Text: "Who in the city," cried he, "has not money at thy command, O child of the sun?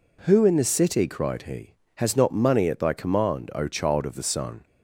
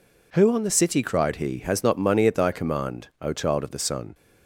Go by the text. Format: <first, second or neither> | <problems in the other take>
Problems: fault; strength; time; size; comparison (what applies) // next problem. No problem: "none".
first | says "on" for "in"; at 0.5 s